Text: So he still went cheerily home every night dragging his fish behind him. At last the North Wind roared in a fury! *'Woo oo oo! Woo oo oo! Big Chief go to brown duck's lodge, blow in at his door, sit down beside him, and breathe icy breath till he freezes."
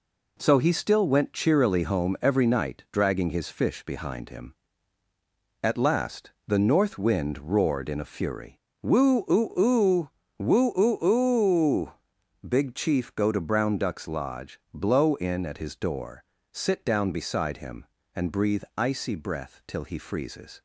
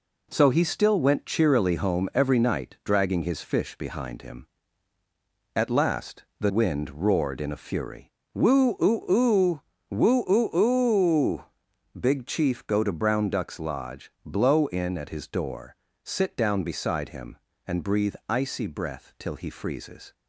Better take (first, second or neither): first